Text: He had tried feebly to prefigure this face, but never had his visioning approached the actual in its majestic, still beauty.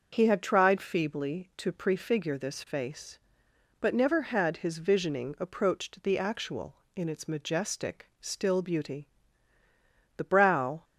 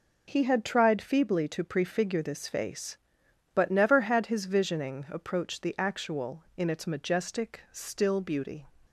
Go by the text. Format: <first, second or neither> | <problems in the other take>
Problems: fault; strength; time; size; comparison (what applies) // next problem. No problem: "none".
second | starts louder than the rest; until 1.1 s; 6.5 dB // goes on to say "The brow"; noticeable; from 10.1 s on; 0.68 s long